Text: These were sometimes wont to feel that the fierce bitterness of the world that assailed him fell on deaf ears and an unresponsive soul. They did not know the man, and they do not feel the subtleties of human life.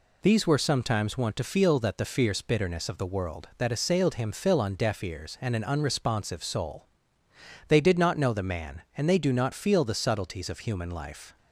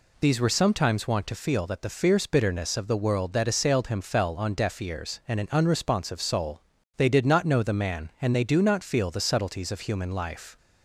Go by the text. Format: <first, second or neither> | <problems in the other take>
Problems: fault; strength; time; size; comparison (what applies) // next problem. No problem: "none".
second | says "fill" for "fell"; at 4.3 s